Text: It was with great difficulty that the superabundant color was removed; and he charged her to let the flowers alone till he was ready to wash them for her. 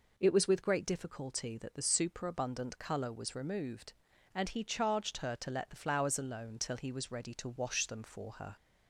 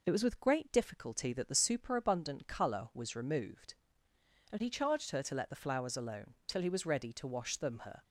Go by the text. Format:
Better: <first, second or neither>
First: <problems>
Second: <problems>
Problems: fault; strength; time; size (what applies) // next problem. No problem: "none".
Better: first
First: none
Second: skips "for"; at 7.7 s